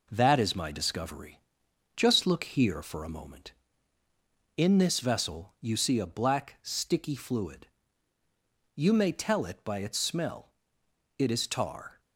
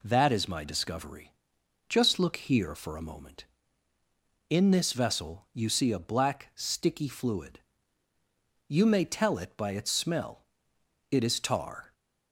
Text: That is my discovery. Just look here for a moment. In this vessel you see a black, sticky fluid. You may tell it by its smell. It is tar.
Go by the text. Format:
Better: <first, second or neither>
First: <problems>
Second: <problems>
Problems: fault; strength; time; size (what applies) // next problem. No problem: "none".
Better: second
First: gets quieter; throughout; 4 dB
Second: none